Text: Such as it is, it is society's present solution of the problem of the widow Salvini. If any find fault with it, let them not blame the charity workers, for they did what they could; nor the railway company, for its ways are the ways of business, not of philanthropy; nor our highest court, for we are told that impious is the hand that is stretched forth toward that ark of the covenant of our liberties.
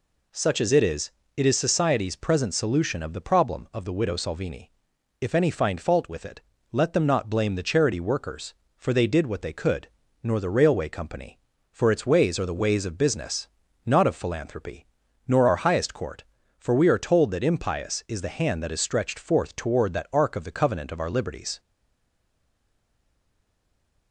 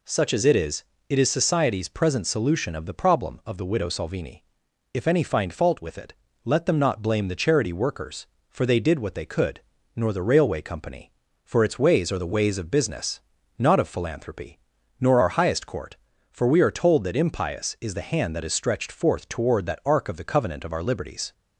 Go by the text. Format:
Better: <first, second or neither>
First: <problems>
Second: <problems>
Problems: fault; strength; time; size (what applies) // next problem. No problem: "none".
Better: second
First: stays silent after the last word; from 21.5 s on; 2.6 s long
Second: none